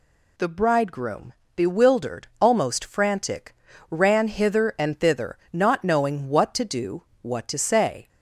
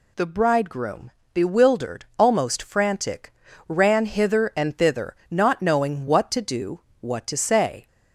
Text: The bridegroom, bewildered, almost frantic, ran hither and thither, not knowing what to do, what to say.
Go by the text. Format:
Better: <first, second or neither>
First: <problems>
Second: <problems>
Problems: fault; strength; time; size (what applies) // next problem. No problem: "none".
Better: neither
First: none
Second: none